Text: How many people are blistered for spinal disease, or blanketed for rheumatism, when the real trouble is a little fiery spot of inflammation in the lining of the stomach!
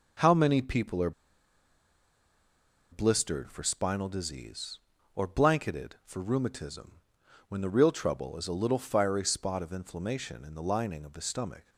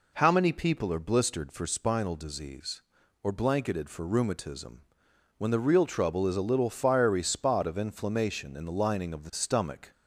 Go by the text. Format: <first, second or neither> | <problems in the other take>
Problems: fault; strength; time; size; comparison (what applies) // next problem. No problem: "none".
second | pauses between "are" and "blistered"; strong; at 1.1 s; 1.7 s long